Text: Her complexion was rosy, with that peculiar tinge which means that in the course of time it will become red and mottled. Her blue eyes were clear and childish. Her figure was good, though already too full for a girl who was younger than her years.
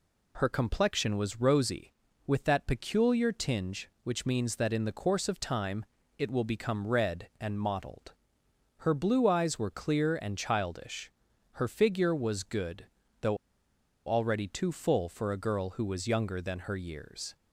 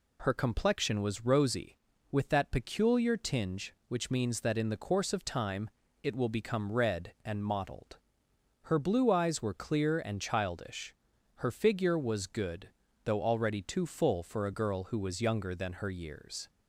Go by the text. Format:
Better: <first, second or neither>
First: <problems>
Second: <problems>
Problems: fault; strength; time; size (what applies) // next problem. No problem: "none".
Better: second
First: pauses between "time" and "it"; slight; at 5.8 s; 0.32 s long // pauses between "though" and "already"; noticeable; at 13.3 s; 0.70 s long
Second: pauses between "time" and "it"; slight; at 5.7 s; 0.32 s long